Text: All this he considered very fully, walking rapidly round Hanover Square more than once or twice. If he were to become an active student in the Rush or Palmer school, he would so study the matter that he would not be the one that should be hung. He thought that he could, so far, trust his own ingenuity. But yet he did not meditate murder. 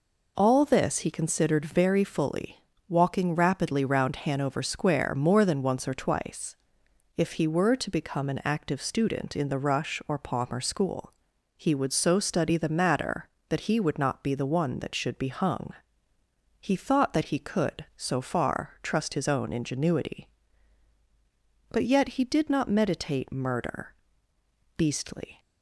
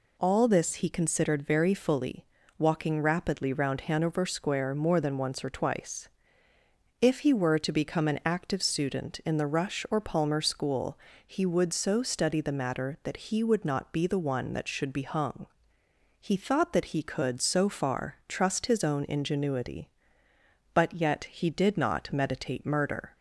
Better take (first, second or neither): second